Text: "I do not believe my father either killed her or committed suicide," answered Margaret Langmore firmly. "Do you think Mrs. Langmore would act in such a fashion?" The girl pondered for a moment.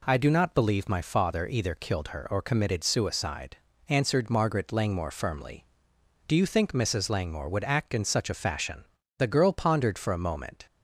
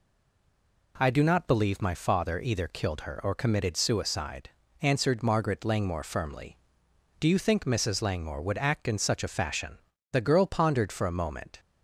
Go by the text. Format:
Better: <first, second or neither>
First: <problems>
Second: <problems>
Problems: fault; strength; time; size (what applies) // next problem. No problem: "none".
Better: first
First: none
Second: stays silent before the first word; slight; until 0.9 s; 0.9 s long